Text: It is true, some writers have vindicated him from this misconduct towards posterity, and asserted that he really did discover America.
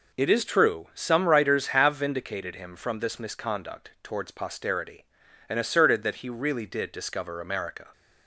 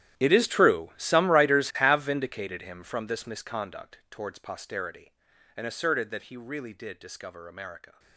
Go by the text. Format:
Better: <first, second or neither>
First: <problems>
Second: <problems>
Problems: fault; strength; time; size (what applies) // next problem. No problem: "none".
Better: first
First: none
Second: gets quieter; strong; throughout; 17.5 dB